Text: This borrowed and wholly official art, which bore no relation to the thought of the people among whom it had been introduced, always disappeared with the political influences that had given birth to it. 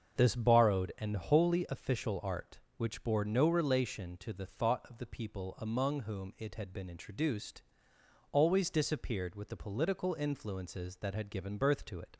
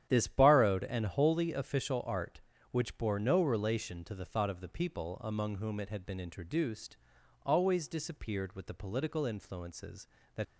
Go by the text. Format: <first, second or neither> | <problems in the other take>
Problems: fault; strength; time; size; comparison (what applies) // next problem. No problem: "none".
first | starts louder than the rest; strong; until 1.1 s; 10 dB; also in the first // stops before "had given birth to it"; at 10.4 s